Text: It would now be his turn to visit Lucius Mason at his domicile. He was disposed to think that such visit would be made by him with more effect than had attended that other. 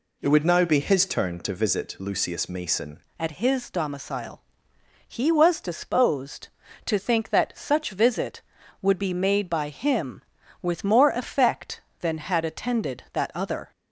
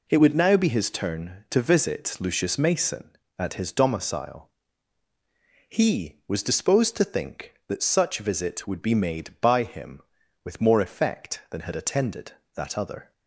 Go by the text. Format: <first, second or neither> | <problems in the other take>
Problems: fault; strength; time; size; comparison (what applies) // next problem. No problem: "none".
second | changes voice at "at"; from 3.1 s on; 10.6 s long